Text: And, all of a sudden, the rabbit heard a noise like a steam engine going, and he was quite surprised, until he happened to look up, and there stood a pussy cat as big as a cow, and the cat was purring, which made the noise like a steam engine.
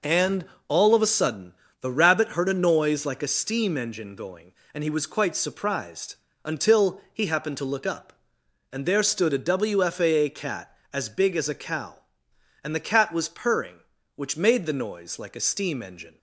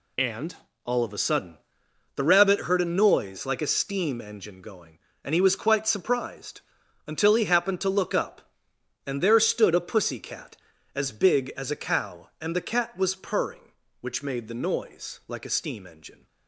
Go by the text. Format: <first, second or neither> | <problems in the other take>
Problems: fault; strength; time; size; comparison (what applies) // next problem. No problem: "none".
second | says "wfaa" for "pussy"; at 9.3 s